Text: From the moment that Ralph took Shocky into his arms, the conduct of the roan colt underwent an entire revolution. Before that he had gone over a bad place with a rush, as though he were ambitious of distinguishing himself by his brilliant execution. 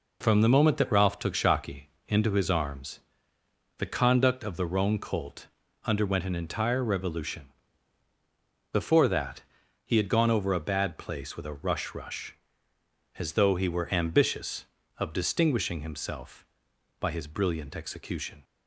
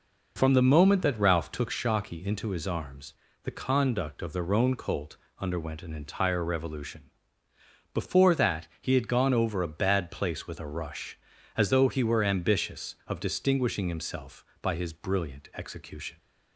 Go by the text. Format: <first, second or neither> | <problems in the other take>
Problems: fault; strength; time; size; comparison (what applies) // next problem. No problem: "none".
second | pauses between "Shocky" and "into"; slight; at 1.8 s; 0.16 s long // pauses between "colt" and "underwent"; slight; at 5.4 s; 0.36 s long; slight in the second // pauses between "that" and "he"; at 9.4 s; 0.42 s long // says "rush" twice; at 11.9 s